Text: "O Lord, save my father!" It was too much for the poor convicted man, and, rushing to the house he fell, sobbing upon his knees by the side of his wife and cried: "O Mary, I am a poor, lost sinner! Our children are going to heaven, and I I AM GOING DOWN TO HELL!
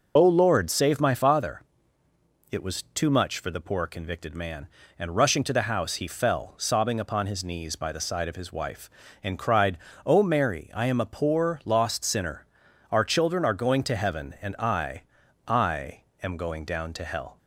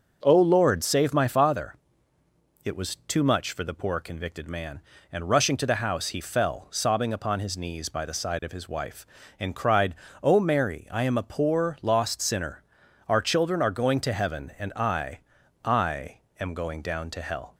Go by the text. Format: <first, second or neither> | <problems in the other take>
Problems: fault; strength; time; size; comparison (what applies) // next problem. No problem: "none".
second | loses the start of "O"; at 0.1 s; 60 ms // pauses between "I" and "I"; at 15.0 s; 0.44 s long; also in the second // pauses between "I" and "AM"; slight; at 16.0 s; 0.20 s long; slight in the second